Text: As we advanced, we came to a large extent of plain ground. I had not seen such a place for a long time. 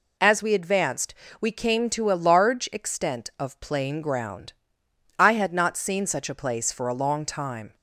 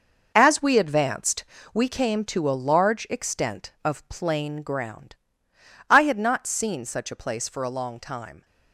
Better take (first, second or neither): first